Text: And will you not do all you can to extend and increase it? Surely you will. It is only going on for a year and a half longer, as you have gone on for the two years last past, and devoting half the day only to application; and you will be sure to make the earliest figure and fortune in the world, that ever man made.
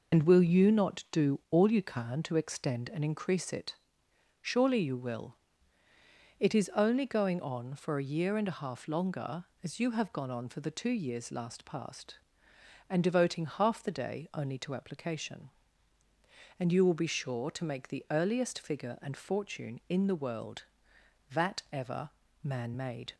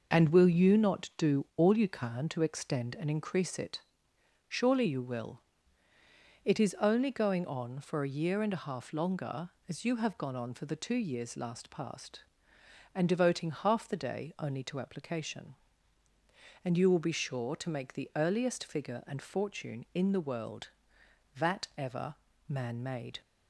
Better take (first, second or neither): second